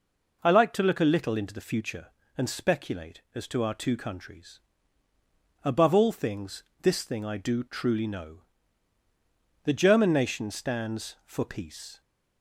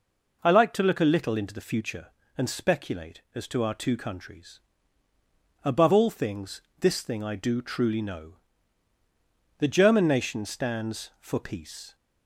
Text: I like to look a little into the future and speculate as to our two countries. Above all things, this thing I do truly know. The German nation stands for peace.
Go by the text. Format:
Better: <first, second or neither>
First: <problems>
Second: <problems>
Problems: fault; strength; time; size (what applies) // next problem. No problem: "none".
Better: neither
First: none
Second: none